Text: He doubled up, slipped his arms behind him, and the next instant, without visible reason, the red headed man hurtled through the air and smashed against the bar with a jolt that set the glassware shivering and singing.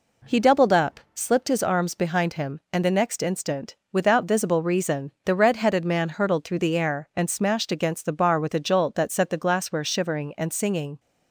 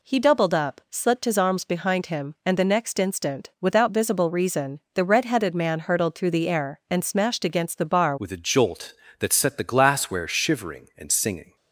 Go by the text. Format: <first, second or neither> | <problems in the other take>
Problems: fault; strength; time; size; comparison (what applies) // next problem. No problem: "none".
first | changes voice at "with"; from 8.1 s on; 3.4 s long